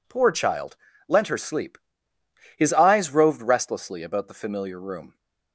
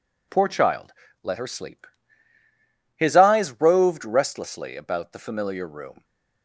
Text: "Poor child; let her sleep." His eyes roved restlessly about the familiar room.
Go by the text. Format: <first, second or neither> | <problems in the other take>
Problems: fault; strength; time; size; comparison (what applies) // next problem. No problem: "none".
second | says "lent" for "let"; at 1.0 s